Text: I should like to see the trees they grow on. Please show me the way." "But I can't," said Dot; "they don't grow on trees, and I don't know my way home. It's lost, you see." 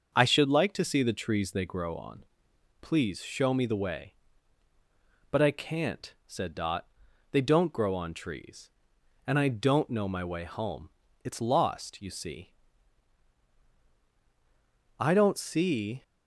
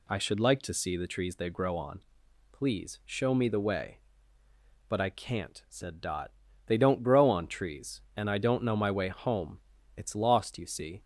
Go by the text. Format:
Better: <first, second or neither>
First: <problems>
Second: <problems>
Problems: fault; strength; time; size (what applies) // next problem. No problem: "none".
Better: second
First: starts louder than the rest; until 1.1 s; 6.5 dB // goes on to say "I don't see"; noticeable; from 14.9 s on; 1.0 s long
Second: none